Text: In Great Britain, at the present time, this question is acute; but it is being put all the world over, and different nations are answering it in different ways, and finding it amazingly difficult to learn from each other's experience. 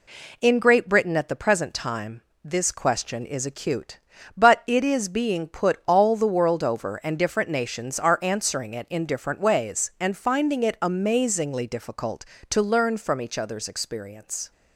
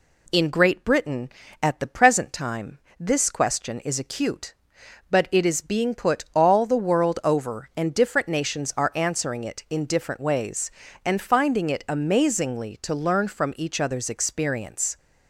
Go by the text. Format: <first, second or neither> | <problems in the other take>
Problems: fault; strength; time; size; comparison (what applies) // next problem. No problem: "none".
first | skips "difficult"; at 12.7 s